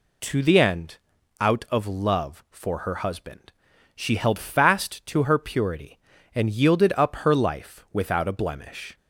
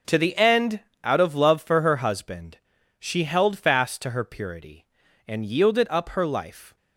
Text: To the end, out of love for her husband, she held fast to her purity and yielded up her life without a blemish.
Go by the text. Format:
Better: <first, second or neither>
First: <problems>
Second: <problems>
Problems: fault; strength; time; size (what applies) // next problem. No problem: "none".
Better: first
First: none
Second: stops before "without a blemish"; at 6.7 s